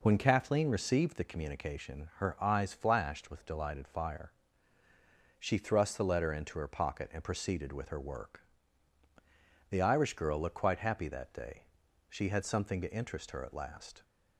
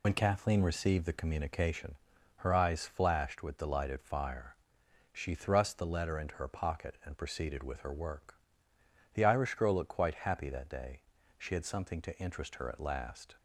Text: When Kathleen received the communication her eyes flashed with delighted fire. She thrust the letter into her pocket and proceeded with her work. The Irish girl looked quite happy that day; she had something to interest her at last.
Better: first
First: none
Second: loses the start of "When"; at 0.0 s; 60 ms // pauses between "communication" and "her"; at 1.9 s; 0.40 s long

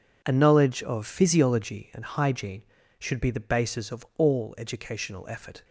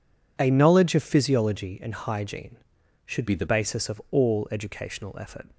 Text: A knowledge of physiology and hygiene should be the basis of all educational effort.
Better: first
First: none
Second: changes voice from "be" to "the"; from 3.2 to 3.4 s; 0.2 s long

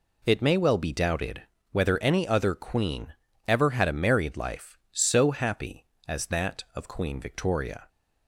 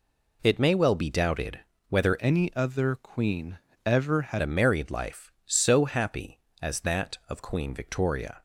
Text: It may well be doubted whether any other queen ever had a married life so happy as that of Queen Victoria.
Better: first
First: pauses between "doubted" and "whether"; slight; at 1.4 s; 0.28 s long // pauses between "queen" and "ever"; slight; at 3.1 s; 0.34 s long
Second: pauses between "doubted" and "whether"; slight; at 1.6 s; 0.28 s long // changes voice from "any" to "had"; from 2.1 to 4.4 s; 2.3 s long // pauses between "queen" and "ever"; slight; at 3.5 s; 0.28 s long

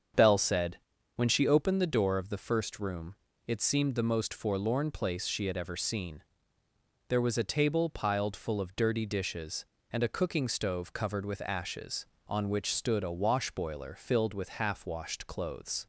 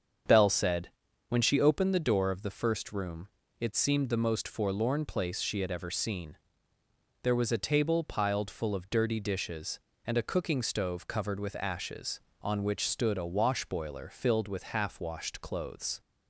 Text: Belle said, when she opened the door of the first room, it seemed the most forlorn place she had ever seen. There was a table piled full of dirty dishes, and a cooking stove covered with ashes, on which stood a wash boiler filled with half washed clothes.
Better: neither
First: starts louder than the rest; strong; until 1.5 s; 7 dB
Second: starts louder than the rest; strong; until 1.6 s; 7.5 dB

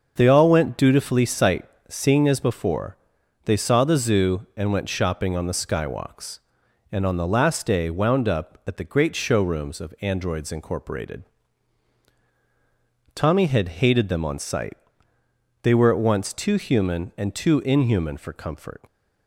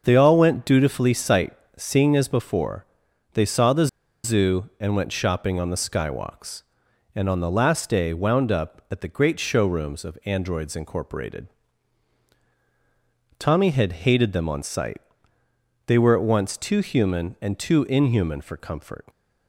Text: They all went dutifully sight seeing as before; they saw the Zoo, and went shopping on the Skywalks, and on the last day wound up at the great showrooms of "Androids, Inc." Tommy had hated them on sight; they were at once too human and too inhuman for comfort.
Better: first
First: starts louder than the rest; until 1.1 s; 6.5 dB // pauses between "sight" and "seeing"; slight; at 1.6 s; 0.24 s long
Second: starts louder than the rest; until 1.0 s; 6.5 dB // pauses between "sight" and "seeing"; slight; at 1.5 s; 0.24 s long // pauses between "the" and "Zoo"; at 3.8 s; 0.37 s long

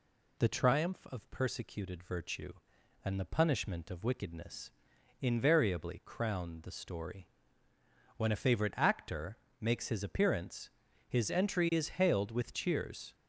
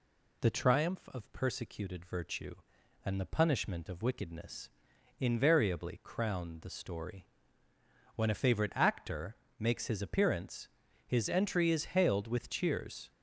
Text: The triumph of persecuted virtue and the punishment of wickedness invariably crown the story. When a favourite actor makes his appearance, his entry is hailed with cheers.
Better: neither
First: pauses between "wickedness" and "invariably"; noticeable; at 4.7 s; 0.48 s long // pauses between "actor" and "makes"; slight; at 9.3 s; 0.22 s long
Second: pauses between "wickedness" and "invariably"; noticeable; at 4.7 s; 0.48 s long // pauses between "actor" and "makes"; slight; at 9.3 s; 0.22 s long

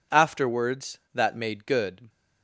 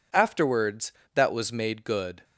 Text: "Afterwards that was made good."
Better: second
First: skips "was"; at 1.3 s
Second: none

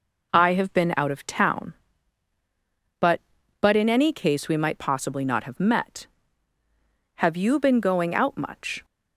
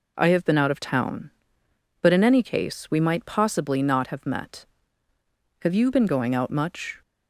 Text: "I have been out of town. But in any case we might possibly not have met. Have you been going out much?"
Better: second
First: says "But" twice; at 3.6 s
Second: none

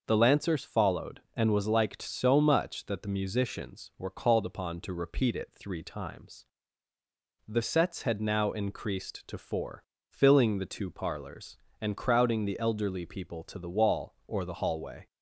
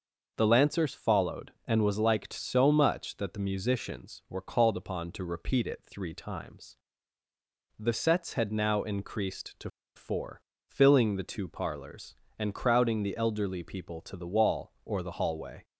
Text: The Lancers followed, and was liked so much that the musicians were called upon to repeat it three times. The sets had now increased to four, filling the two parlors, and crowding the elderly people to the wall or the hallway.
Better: first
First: none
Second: pauses between "to" and "four"; slight; at 9.6 s; 0.25 s long

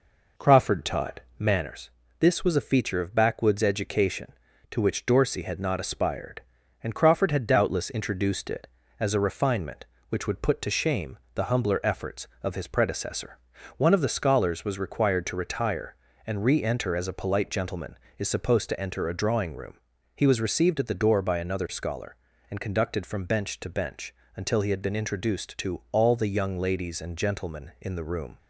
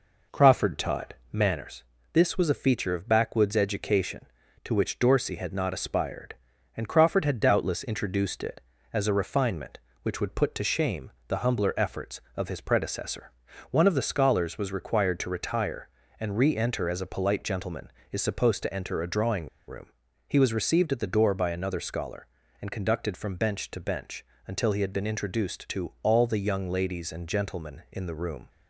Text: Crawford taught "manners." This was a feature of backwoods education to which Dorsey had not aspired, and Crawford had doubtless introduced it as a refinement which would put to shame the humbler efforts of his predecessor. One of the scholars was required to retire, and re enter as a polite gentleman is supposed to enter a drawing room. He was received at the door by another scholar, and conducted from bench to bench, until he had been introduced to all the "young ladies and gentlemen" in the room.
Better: first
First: pauses between "taught" and "manners"; slight; at 1.1 s; 0.18 s long // pauses between "shame" and "the"; slight; at 11.1 s; 0.16 s long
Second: pauses between "taught" and "manners"; slight; at 1.1 s; 0.18 s long // pauses between "shame" and "the"; slight; at 11.1 s; 0.16 s long // pauses between "drawing" and "room"; slight; at 19.4 s; 0.19 s long

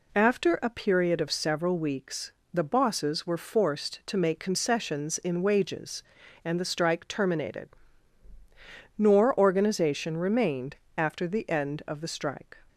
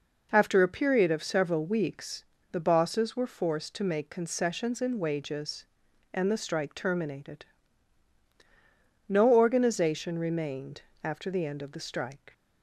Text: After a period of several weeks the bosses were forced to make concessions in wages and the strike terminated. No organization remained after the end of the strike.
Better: second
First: pauses between "weeks" and "the"; slight; at 2.3 s; 0.20 s long // says "Nor" for "No"; at 8.9 s // pauses between "remained" and "after"; slight; at 10.7 s; 0.22 s long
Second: pauses between "weeks" and "the"; slight; at 2.2 s; 0.26 s long // pauses between "remained" and "after"; slight; at 10.8 s; 0.20 s long

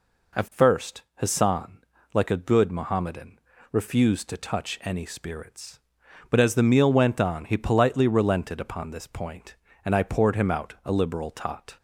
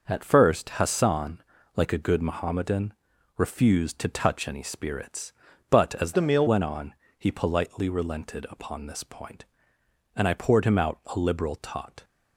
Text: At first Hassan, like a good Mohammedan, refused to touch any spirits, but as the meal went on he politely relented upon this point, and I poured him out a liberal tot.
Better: first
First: none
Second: changes voice from "the" to "meal"; from 6.1 to 6.4 s; 0.3 s long // pauses between "on" and "he"; slight; at 6.9 s; 0.24 s long

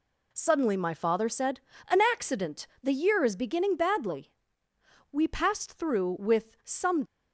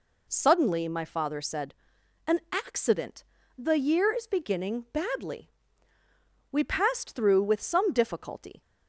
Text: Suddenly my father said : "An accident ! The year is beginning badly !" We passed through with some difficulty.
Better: second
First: stops before "difficulty"; at 7.0 s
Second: none

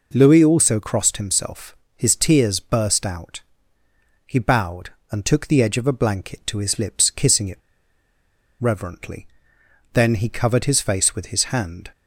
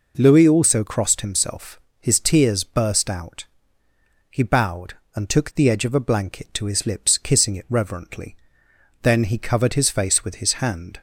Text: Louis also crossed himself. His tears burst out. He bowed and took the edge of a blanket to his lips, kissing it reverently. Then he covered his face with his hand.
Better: second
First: pauses between "it" and "reverently"; at 7.5 s; 1.0 s long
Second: none

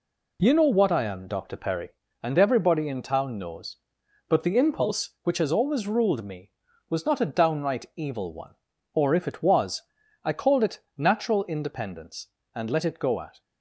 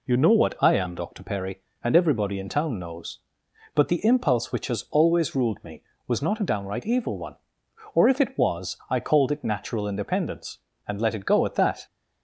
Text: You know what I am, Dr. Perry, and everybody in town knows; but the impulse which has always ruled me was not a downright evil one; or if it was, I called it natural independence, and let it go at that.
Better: second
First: pauses between "it" and "natural"; slight; at 10.7 s; 0.18 s long // stops before "that"; at 13.4 s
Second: none

